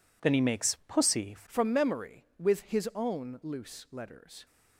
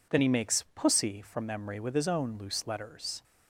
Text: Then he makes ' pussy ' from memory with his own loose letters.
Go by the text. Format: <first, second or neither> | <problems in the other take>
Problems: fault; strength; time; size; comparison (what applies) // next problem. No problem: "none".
second | changes voice at "from"; from 1.4 s on; 3.0 s long